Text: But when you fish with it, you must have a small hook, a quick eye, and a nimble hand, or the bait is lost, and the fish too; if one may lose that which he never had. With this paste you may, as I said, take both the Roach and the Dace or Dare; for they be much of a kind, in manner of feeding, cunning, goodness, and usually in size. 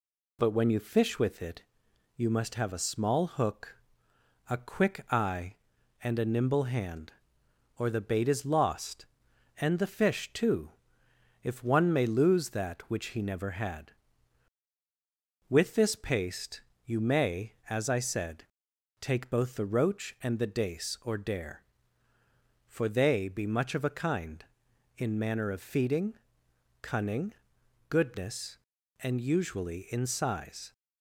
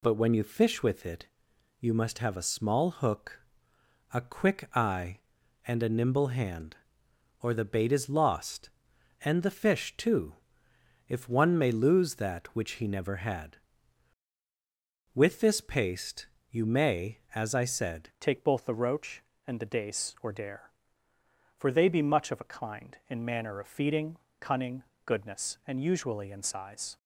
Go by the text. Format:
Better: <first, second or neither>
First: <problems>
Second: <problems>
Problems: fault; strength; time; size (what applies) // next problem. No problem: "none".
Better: first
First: pauses between "paste" and "you"; slight; at 16.6 s; 0.24 s long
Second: pauses between "paste" and "you"; slight; at 16.2 s; 0.24 s long // changes voice at "take"; from 18.1 s on; 8.8 s long